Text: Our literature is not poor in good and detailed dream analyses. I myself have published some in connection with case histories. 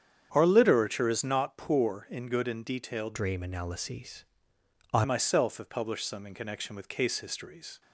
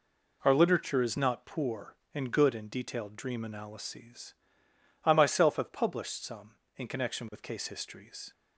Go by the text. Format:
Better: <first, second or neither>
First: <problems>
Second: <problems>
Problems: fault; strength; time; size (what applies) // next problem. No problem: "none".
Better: second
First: starts louder than the rest; strong; until 1.3 s; 8 dB // changes voice from "dream" to "I"; from 3.1 to 5.0 s; 1.9 s long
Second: none